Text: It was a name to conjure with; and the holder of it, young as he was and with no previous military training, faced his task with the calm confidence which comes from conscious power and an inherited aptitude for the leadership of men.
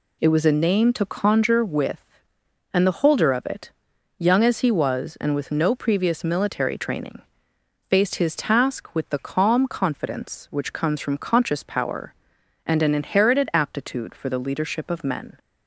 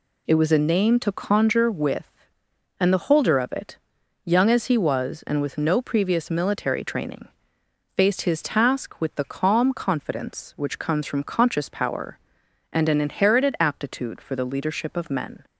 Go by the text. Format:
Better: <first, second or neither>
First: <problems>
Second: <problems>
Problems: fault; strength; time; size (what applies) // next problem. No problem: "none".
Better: neither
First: none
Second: none